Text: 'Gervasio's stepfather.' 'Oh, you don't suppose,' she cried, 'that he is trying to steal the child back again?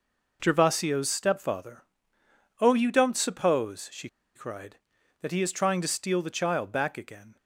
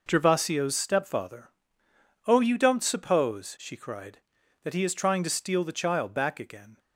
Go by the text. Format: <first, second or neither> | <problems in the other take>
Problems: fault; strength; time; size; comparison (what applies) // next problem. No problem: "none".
second | pauses between "she" and "cried"; slight; at 4.0 s; 0.26 s long